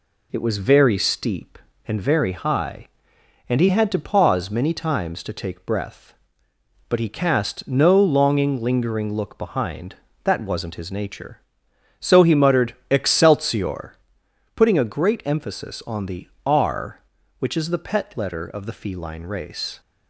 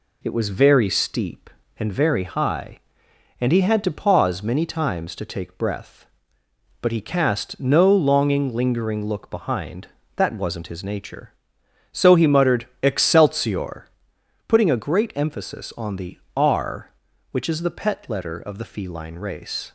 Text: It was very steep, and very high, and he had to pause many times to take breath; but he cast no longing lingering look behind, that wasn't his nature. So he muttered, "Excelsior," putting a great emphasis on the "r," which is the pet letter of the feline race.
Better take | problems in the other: neither | pauses between "the" and "r"; slight; the same in both

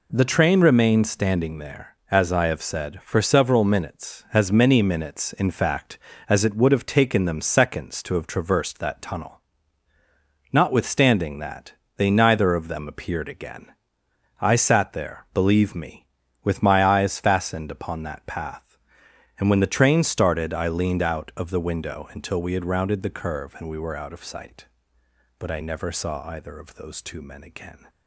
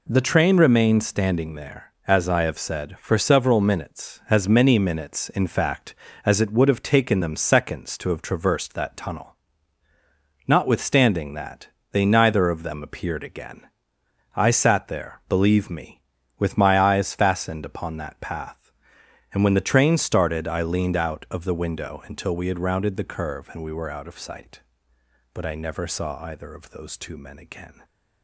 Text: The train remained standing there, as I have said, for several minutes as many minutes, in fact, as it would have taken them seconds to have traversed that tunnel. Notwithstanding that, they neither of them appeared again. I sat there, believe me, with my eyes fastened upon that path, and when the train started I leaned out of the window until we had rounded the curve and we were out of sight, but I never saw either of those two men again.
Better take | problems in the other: neither | none

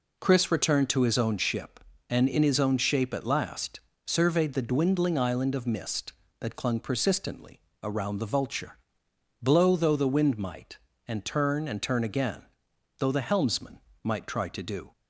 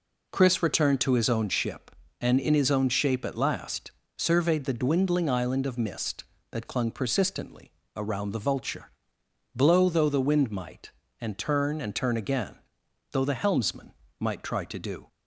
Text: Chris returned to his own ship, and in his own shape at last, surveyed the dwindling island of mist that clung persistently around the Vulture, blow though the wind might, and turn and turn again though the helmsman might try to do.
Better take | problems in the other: neither | pauses between "persistently" and "around"; slight; the same in both // pauses between "again" and "though"; noticeable; the same in both // pauses between "helmsman" and "might"; slight; the same in both

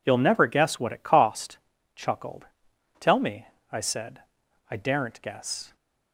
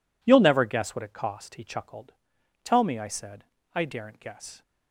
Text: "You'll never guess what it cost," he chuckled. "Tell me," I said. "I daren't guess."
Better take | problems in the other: second | skips "he"; at 1.7 s

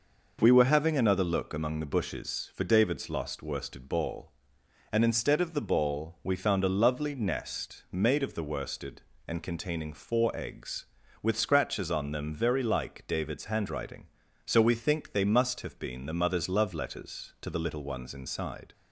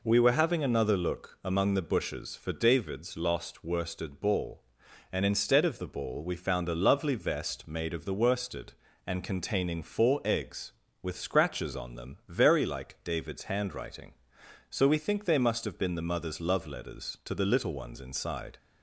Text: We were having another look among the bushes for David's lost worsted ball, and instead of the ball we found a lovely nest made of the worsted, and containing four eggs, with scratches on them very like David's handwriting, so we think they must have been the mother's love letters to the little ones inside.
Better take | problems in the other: first | says "vest" for "nest"; at 7.1 s

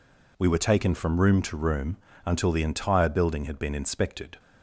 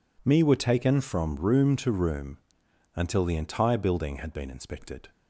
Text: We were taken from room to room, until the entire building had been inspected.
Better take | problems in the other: first | says "Me" for "We"; at 0.2 s

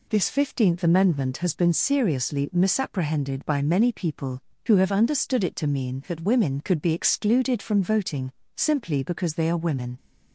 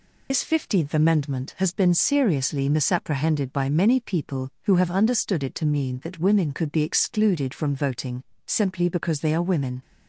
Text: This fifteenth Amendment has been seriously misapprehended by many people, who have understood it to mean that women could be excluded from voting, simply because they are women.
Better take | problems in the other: first | loses the start of "This"; at 0.3 s; 85 ms

